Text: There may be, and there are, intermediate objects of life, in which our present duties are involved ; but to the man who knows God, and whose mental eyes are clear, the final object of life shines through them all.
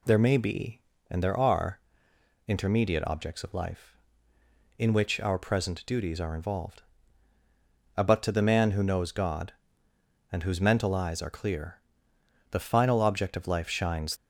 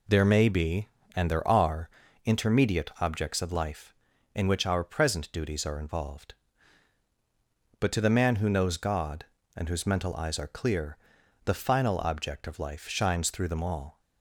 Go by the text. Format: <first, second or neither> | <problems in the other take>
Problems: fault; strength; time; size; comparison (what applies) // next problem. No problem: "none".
second | stops before "through them all"; at 14.1 s